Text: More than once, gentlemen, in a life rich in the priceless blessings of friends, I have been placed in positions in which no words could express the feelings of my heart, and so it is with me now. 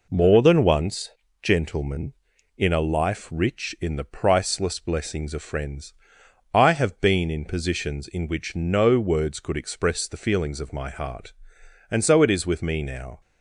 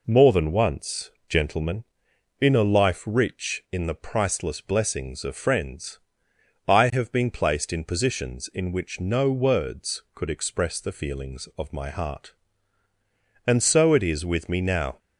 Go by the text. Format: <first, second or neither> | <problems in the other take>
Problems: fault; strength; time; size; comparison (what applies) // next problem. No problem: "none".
second | skips "placed"; at 7.2 s